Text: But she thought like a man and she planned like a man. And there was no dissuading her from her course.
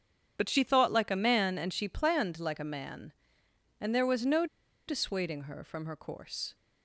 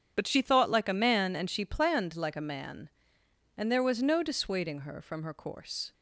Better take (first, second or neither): second